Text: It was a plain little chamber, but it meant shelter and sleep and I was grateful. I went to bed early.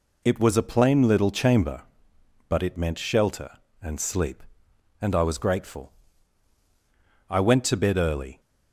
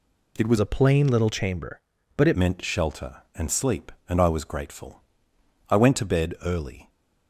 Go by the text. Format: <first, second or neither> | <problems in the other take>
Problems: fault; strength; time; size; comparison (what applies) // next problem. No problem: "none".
first | changes voice from "a" to "it"; from 0.5 to 2.3 s; 1.8 s long